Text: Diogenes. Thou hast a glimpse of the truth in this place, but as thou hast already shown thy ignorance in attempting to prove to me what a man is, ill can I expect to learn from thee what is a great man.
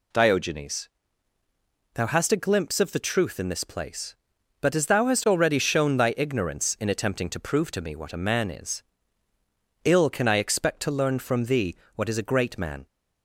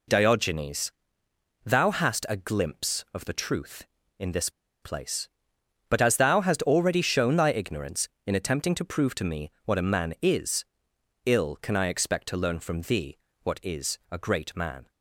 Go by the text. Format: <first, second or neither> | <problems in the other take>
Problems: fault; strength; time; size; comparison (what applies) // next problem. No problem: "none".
first | pauses between "this" and "place"; slight; at 4.4 s; 0.33 s long // pauses between "thee" and "what"; slight; at 13.1 s; 0.26 s long; slight in the first